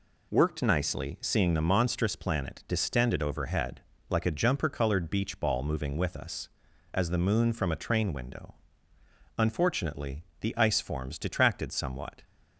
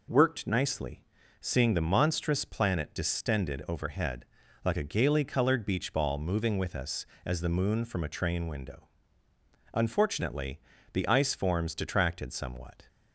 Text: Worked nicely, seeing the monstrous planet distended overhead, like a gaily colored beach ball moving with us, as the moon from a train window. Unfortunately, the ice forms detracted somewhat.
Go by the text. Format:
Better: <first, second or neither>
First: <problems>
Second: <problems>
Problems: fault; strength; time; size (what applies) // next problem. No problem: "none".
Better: second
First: says "jumper" for "gaily"; at 4.3 s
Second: none